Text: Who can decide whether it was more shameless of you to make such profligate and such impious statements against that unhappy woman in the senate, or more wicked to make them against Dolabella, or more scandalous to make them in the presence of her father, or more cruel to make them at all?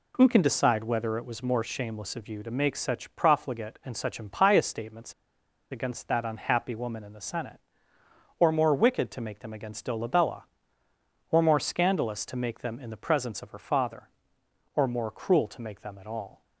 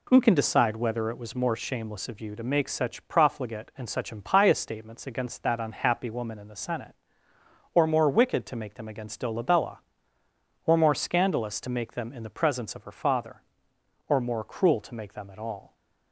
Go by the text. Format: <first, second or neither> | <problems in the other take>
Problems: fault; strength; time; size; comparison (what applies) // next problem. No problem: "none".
second | pauses between "statements" and "against"; noticeable; at 5.1 s; 0.57 s long